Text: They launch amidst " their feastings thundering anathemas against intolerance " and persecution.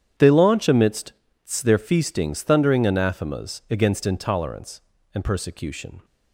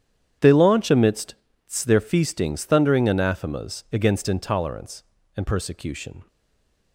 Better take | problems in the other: first | starts louder than the rest; strong; until 1.6 s; 10 dB; strong in the first // stays silent after the last word; slight; from 6.2 s on; 0.7 s long

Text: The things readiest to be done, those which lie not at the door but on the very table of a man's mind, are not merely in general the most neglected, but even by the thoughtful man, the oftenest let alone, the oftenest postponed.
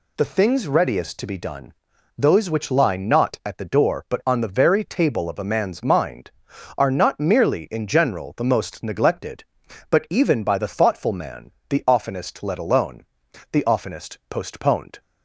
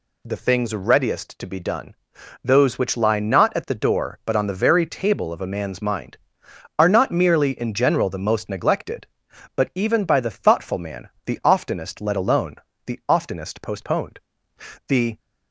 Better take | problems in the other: first | goes on to say "The"; slight; from 14.8 s on; 0.32 s long

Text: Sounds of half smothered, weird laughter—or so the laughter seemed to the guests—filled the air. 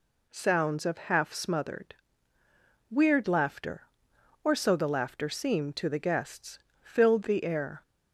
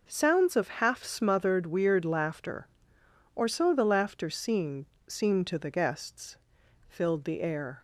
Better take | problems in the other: first | says "seemed" twice; at 5.0 s

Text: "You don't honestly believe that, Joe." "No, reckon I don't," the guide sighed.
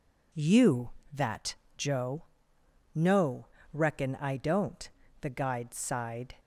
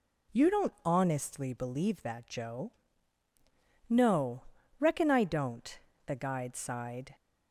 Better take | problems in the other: second | skips "don't honestly believe"; at 1.0 s

